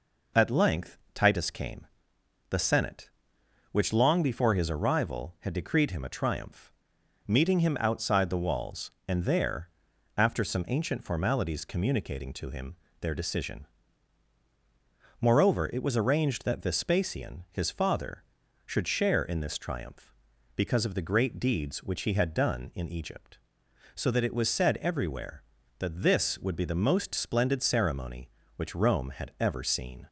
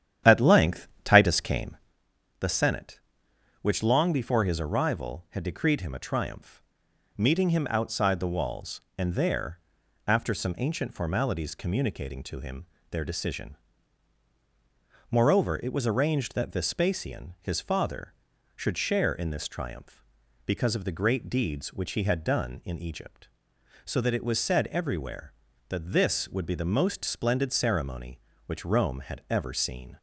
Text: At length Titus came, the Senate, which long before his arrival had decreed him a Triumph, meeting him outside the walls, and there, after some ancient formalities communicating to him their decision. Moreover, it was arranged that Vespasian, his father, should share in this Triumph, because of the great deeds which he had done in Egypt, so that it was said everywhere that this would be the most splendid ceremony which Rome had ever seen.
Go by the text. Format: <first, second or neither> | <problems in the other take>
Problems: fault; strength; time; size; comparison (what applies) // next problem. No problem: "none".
first | starts louder than the rest; strong; until 2.0 s; 10.5 dB // pauses between "length" and "Titus"; slight; at 0.8 s; 0.16 s long; slight in the first // pauses between "him" and "their"; slight; at 12.6 s; 0.26 s long; slight in the first